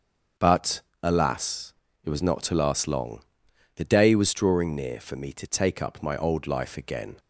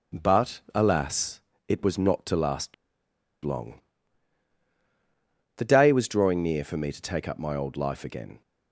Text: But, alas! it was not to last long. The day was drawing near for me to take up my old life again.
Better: first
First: starts louder than the rest; until 1.5 s; 6.5 dB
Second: starts louder than the rest; until 1.2 s; 7 dB // pauses between "last" and "long"; noticeable; at 2.7 s; 0.70 s long

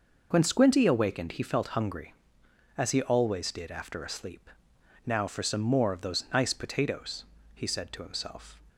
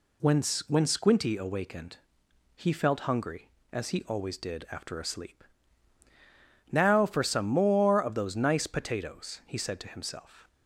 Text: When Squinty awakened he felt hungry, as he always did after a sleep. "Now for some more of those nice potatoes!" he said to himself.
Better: first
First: none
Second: says "When" twice; at 0.6 s // pauses between "awakened" and "he"; noticeable; at 1.9 s; 0.58 s long

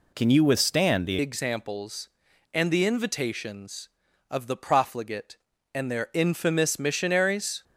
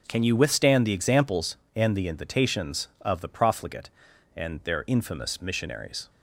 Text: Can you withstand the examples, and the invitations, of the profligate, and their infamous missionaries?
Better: second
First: changes voice at "examples"; from 1.1 s on; 6.5 s long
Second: none

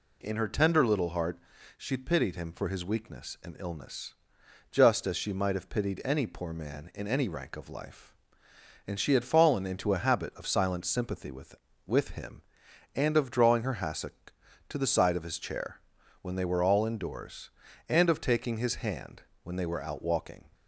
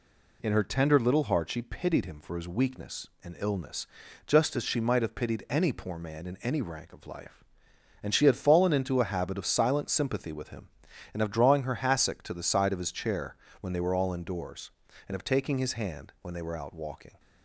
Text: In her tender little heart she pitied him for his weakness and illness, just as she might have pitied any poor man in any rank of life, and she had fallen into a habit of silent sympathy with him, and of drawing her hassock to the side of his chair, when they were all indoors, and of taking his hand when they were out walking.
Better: second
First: pauses between "heart" and "she"; at 1.3 s; 0.38 s long // says "with" twice; at 11.8 s // pauses between "hand" and "when"; slight; at 19.2 s; 0.22 s long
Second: none

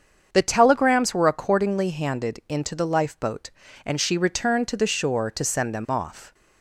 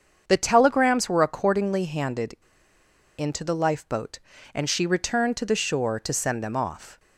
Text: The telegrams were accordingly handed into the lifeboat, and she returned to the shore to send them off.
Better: first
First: starts louder than the rest; strong; until 1.3 s; 7 dB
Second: starts louder than the rest; strong; until 1.2 s; 7 dB // pauses between "handed" and "into"; noticeable; at 2.3 s; 0.81 s long

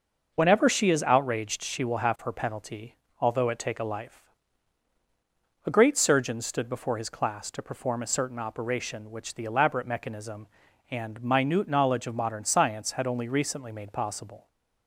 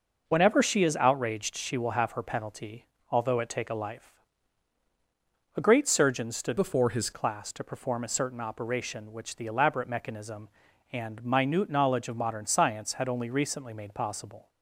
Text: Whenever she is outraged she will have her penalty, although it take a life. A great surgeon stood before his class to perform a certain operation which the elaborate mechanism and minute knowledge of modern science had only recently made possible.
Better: first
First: none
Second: changes voice from "before" to "his"; from 6.5 to 7.1 s; 0.6 s long

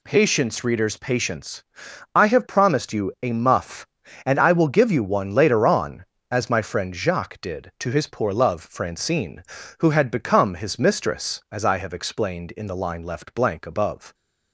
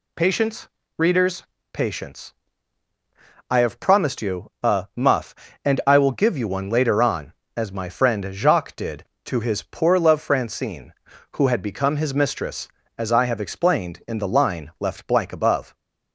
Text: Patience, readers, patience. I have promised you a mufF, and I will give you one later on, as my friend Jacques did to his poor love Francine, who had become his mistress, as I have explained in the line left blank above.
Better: neither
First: none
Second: none

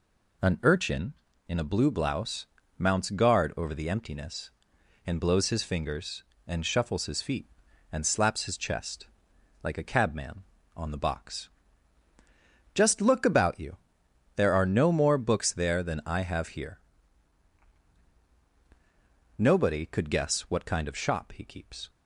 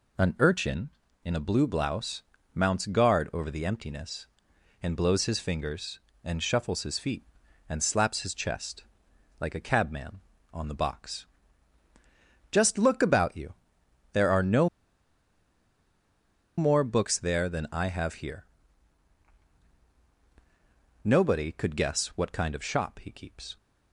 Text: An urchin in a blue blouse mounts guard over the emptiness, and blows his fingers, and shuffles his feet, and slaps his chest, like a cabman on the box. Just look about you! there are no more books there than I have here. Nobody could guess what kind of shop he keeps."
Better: first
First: pauses between "blouse" and "mounts"; slight; at 2.4 s; 0.32 s long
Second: pauses between "blouse" and "mounts"; slight; at 2.2 s; 0.32 s long // pauses between "no" and "more"; strong; at 14.6 s; 1.8 s long

